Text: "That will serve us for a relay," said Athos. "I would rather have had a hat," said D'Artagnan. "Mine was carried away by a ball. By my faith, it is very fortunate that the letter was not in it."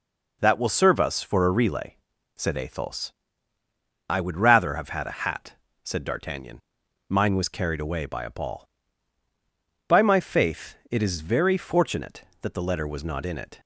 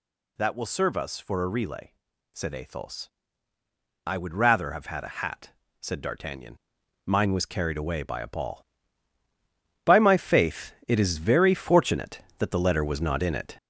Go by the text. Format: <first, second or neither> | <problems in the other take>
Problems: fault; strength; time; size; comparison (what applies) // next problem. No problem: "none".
first | gets louder; throughout; 6.5 dB